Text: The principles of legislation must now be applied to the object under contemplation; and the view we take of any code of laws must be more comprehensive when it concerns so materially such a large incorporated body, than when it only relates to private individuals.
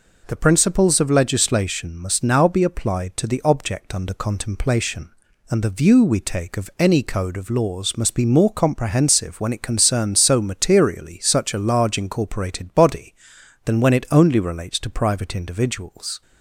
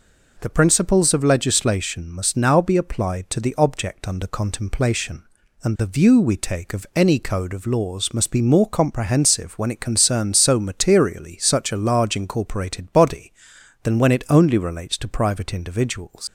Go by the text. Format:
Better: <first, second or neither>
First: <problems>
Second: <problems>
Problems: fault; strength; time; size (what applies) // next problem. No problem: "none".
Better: first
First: none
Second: leaves "individuals" unfinished; at 16.2 s; 120 ms